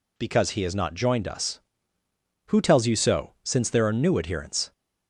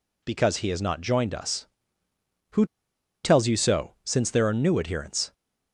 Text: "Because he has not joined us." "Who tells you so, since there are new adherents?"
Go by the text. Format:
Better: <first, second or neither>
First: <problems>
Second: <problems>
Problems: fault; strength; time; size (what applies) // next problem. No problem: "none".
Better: first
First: none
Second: pauses between "Who" and "tells"; noticeable; at 2.6 s; 0.59 s long